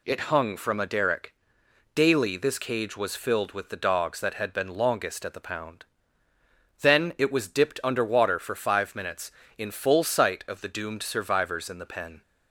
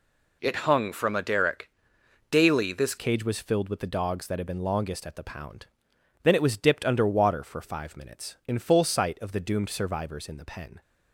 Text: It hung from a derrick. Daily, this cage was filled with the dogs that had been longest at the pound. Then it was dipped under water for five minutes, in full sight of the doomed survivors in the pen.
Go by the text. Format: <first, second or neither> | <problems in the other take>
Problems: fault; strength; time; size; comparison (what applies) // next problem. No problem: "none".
first | changes voice at "cage"; from 2.9 s on; 7.9 s long